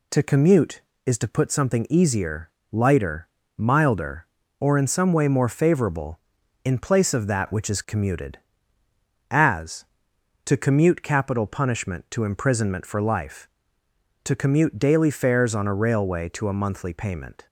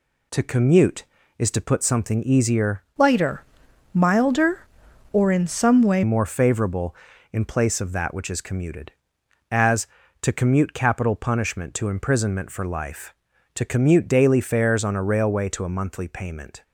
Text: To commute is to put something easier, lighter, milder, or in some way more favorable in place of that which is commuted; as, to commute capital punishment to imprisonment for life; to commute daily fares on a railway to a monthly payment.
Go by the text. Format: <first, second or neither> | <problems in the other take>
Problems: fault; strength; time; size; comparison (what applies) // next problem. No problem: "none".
first | changes voice from "lighter" to "way"; from 2.9 to 6.0 s; 3.1 s long